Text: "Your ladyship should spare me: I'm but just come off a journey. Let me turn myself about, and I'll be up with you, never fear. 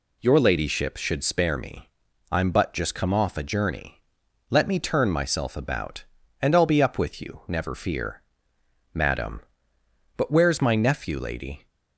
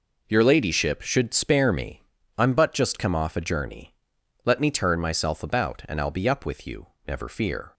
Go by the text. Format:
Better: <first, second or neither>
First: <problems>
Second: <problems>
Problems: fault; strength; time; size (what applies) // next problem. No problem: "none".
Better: second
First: goes on to say "Madam But where's my nephew Lady"; strong; from 8.9 s on; 2.7 s long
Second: none